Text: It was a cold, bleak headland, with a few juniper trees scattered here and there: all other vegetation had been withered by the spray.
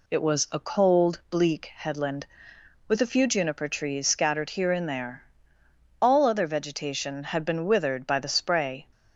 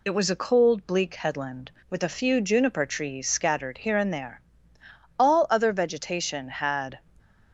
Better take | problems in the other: first | stops before "been withered by the spray"; at 7.1 s

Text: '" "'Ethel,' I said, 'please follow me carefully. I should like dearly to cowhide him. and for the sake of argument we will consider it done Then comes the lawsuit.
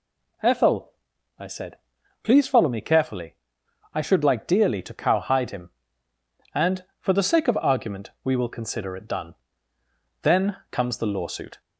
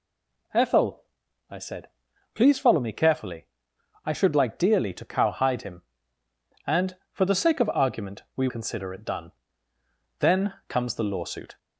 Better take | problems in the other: first | stays silent before the first word; slight; until 0.5 s; 0.5 s long // skips "will"; at 8.4 s // pauses between "done" and "Then"; noticeable; at 9.3 s; 0.88 s long; noticeable in the first // pauses between "Then" and "comes"; slight; at 10.5 s; 0.16 s long; slight in the first

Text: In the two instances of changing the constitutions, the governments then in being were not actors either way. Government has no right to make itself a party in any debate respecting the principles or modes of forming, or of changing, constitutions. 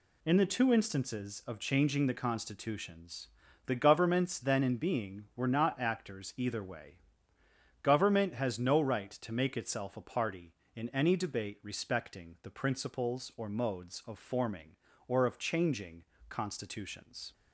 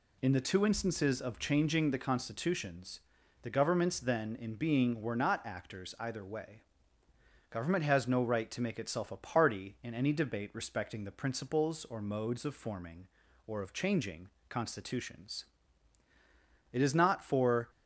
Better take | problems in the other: first | goes on to say "It is not for"; noticeable; from 16.7 s on; 0.96 s long

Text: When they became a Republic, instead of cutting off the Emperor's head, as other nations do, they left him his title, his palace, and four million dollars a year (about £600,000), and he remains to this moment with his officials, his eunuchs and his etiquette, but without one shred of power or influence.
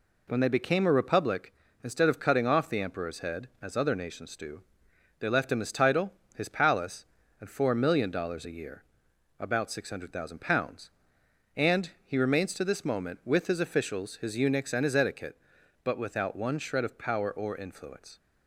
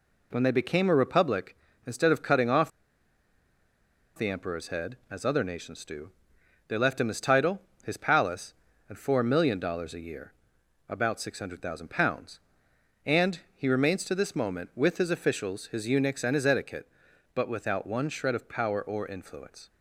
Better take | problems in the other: first | pauses between "off" and "the"; strong; at 2.7 s; 1.4 s long

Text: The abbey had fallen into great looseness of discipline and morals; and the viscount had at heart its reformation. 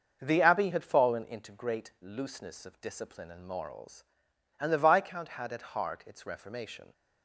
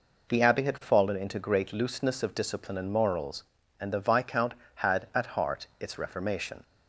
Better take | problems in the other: second | starts louder than the rest; noticeable; until 1.3 s; 6 dB

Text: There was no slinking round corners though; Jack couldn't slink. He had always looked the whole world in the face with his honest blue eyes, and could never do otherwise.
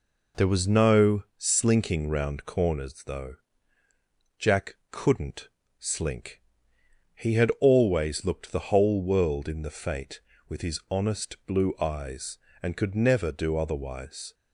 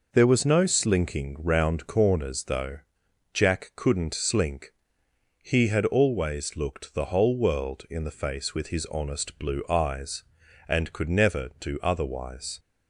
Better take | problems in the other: second | pauses between "Jack" and "couldn't"; slight; at 4.7 s; 0.16 s long // pauses between "couldn't" and "slink"; slight; at 5.4 s; 0.32 s long // says "fate" for "face"; at 9.6 s

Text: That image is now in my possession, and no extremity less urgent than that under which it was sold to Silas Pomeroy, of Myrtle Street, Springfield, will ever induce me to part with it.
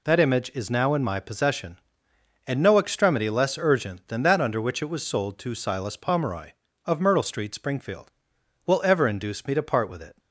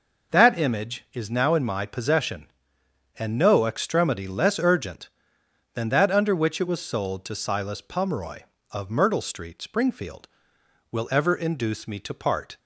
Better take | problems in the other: first | stops before "with it"; at 12.5 s

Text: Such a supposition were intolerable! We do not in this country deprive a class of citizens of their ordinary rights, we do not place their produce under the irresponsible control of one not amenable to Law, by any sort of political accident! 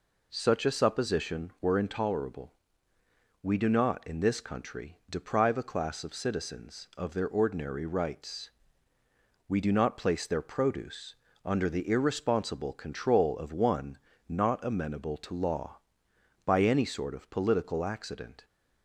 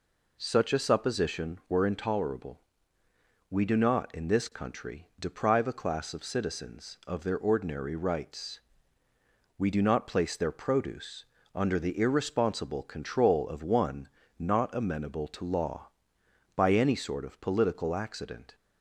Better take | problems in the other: neither | pauses between "produce" and "under"; slight; the same in both // pauses between "one" and "not"; slight; the same in both

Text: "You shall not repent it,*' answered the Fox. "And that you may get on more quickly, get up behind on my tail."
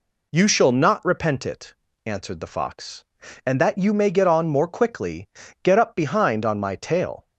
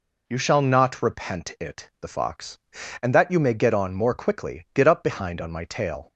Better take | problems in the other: first | skips "answered"; at 1.9 s

